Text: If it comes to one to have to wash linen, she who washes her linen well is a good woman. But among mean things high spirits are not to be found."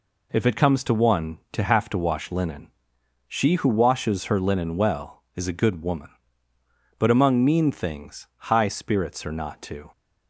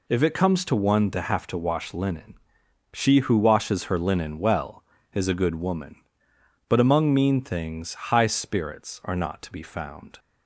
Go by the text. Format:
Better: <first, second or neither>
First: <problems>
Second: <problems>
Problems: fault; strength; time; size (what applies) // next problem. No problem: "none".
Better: second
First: stops before "be found"; at 9.9 s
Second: none